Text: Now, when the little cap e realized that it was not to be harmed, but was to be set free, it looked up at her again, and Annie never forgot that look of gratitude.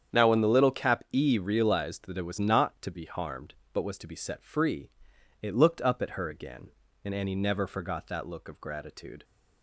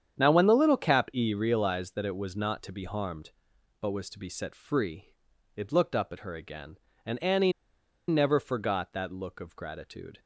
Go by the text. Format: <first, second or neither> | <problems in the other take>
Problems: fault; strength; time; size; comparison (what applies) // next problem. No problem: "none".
first | starts louder than the rest; strong; until 1.2 s; 8.5 dB; strong in the first // pauses between "Annie" and "never"; noticeable; at 7.5 s; 0.56 s long